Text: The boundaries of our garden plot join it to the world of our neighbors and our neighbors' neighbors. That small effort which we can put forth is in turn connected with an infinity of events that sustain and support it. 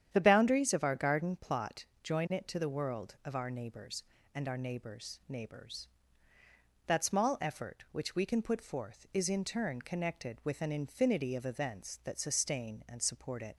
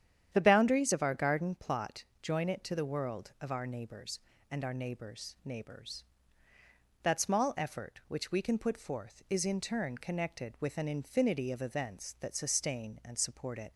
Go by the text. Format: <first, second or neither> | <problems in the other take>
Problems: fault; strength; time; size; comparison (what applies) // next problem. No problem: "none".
neither | starts louder than the rest; strong; the same in both // pauses between "plot" and "join"; slight; the same in both